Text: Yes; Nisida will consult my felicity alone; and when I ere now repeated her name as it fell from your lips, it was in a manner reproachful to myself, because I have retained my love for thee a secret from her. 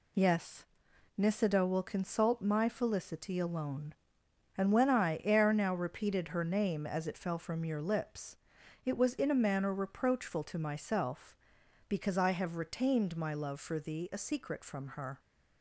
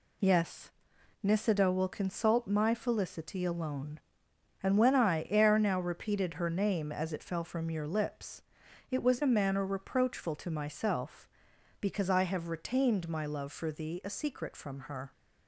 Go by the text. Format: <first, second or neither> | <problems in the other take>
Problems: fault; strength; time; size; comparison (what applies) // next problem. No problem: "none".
first | skips "in"; at 9.2 s